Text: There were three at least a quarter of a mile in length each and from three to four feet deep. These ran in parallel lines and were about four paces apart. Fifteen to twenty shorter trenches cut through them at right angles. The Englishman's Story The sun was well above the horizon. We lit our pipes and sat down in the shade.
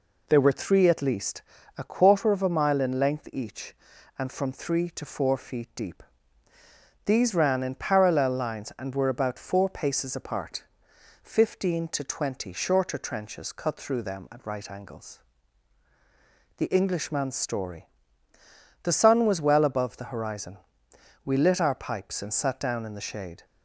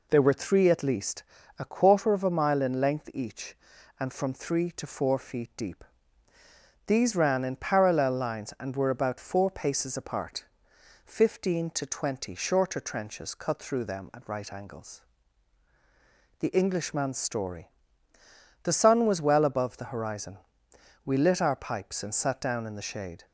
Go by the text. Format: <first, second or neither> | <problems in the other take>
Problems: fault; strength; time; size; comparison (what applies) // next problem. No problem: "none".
neither | pauses between "least" and "a"; slight; the same in both // pauses between "Story" and "The"; noticeable; the same in both